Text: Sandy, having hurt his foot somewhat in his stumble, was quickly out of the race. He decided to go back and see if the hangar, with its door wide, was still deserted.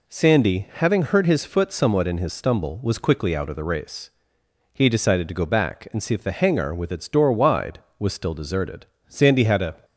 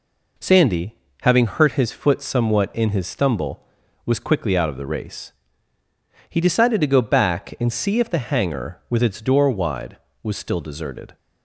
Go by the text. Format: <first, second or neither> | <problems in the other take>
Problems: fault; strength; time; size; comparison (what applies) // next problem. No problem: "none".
second | goes on to say "Sandy had a"; noticeable; from 9.0 s on; 0.68 s long